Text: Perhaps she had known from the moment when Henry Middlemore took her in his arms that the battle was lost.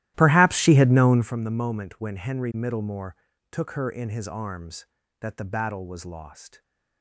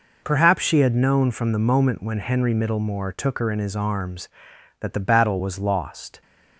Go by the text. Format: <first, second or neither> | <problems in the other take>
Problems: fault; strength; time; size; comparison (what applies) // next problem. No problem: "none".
second | starts louder than the rest; strong; until 1.4 s; 14.5 dB // pauses between "Middlemore" and "took"; slight; at 3.1 s; 0.36 s long